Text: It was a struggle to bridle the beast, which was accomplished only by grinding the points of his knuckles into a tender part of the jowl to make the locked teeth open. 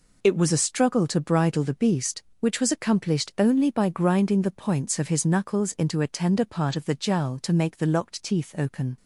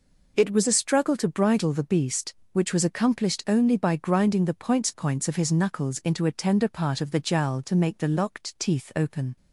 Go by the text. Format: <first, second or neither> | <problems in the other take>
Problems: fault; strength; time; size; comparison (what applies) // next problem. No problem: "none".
first | says "points" twice; at 4.8 s